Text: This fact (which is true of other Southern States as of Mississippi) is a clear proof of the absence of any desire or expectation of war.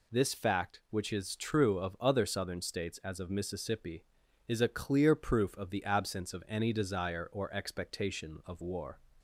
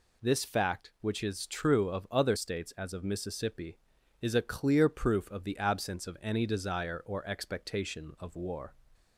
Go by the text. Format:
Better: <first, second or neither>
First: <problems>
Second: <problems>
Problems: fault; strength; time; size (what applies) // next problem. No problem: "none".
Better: first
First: none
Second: skips "Southern"; at 2.3 s